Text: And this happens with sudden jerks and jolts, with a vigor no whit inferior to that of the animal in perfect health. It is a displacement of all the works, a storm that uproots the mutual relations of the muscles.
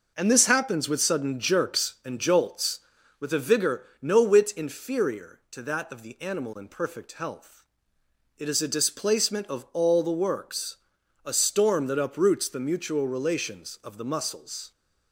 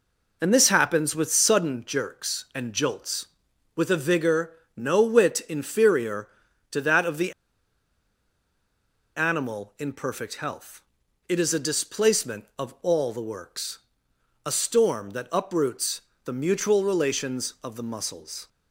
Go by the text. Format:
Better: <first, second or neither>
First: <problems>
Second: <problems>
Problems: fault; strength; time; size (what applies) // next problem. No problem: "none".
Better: first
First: pauses between "vigor" and "no"; slight; at 3.8 s; 0.18 s long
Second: pauses between "vigor" and "no"; slight; at 4.5 s; 0.24 s long // pauses between "the" and "animal"; strong; at 7.3 s; 1.8 s long // pauses between "uproots" and "the"; slight; at 16.0 s; 0.24 s long